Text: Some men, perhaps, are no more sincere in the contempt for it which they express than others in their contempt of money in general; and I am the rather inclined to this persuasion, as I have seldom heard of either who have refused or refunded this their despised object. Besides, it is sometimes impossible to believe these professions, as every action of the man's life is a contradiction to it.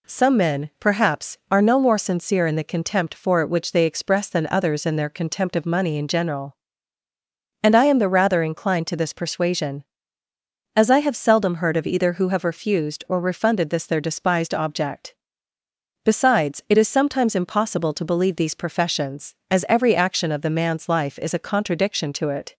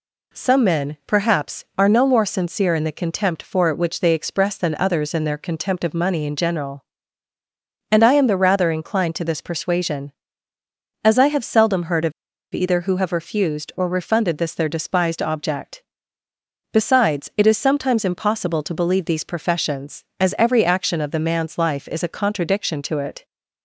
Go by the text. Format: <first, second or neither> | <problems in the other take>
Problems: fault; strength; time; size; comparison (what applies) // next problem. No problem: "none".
first | pauses between "of" and "either"; at 12.1 s; 0.42 s long